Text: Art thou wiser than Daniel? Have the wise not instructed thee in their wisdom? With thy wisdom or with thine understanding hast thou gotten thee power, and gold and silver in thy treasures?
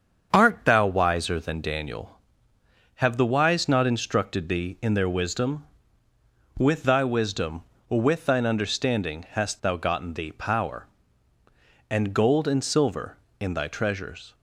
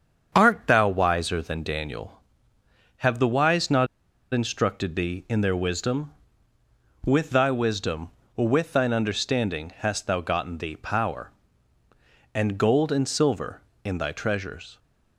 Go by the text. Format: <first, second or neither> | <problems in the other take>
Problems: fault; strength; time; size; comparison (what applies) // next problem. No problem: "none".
first | starts louder than the rest; strong; until 1.3 s; 7.5 dB; strong in the first // pauses between "not" and "instructed"; at 3.8 s; 0.45 s long